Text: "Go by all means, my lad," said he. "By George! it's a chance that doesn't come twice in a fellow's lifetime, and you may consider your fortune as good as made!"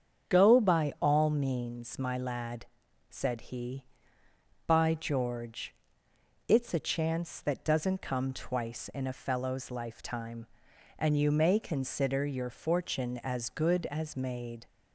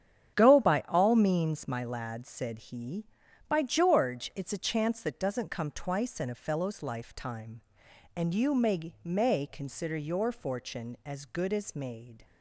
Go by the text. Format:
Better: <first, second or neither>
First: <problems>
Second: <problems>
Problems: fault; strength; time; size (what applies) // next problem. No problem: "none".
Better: first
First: starts louder than the rest; strong; until 1.3 s; 7.5 dB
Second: starts louder than the rest; strong; until 1.4 s; 8.5 dB // says "may" twice; at 9.0 s